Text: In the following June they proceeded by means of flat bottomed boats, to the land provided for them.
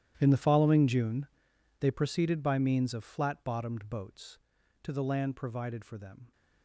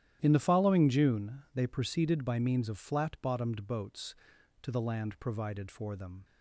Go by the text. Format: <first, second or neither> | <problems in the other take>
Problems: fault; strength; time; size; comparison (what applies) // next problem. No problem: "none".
second | gets quieter; strong; throughout; 19 dB // starts louder than the rest; strong; until 1.1 s; 11.5 dB; strong in the second // pauses between "June" and "they"; noticeable; at 1.2 s; 0.54 s long